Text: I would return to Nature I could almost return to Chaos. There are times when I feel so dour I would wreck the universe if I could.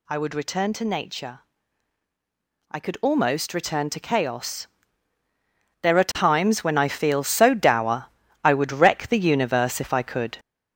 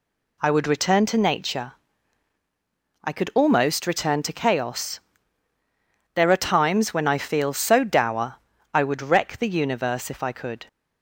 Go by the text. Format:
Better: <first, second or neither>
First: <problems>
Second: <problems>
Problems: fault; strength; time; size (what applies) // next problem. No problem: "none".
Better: second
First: gets louder; noticeable; throughout; 5 dB // pauses between "Nature" and "I"; strong; at 1.4 s; 1.3 s long // pauses between "dour" and "I"; at 8.0 s; 0.38 s long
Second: pauses between "Nature" and "I"; strong; at 1.7 s; 1.3 s long // pauses between "dour" and "I"; at 8.3 s; 0.38 s long